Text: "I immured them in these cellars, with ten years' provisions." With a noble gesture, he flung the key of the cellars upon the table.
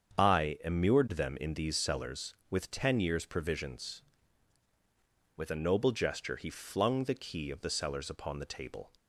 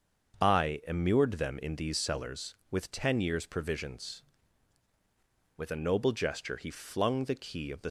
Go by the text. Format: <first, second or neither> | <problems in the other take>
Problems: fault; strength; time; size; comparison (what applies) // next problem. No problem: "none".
first | starts louder than the rest; until 1.4 s; 7 dB; strong in the first // stops before "cellars upon the table"; at 7.8 s